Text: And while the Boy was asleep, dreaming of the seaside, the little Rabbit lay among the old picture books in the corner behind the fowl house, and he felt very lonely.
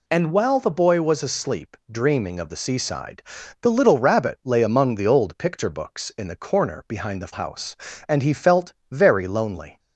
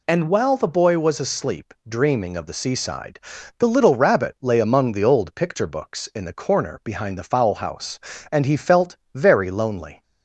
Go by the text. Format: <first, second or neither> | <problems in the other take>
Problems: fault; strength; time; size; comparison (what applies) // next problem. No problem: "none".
second | skips "fowl"; at 7.3 s // pauses between "felt" and "very"; slight; at 8.7 s; 0.18 s long; slight in the second